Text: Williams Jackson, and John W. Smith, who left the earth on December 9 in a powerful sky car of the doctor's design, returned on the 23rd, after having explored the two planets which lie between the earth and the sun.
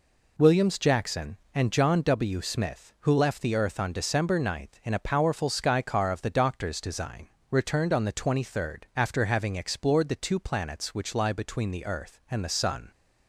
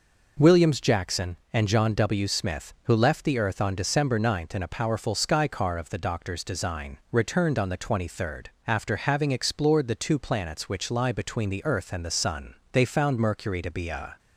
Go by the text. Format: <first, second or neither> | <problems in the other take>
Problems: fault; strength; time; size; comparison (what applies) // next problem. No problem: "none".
first | goes on to say "They found Mercury to be a"; from 12.7 s on; 1.4 s long